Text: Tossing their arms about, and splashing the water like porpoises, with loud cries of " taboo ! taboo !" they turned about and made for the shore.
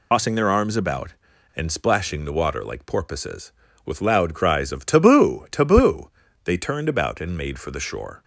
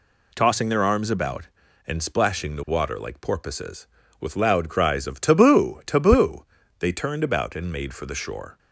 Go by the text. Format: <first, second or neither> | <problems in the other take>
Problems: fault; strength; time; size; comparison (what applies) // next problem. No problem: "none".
second | loses the start of "Tossing"; at 0.1 s; 110 ms